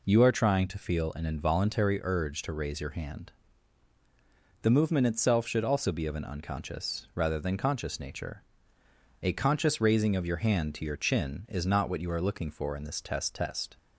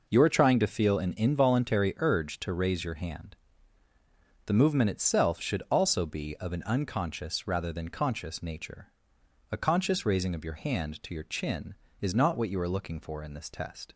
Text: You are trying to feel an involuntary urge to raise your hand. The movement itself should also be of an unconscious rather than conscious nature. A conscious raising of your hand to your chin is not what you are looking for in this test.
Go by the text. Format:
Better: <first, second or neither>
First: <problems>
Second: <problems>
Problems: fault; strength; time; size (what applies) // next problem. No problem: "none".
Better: second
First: says "test" twice; at 13.3 s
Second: none